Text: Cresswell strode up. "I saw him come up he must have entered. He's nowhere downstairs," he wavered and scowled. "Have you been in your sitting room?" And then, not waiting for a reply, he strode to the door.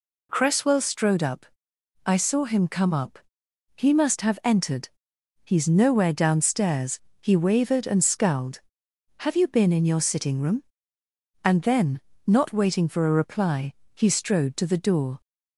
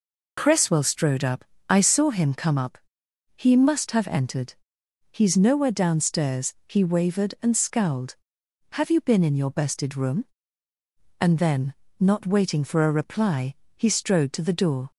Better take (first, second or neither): first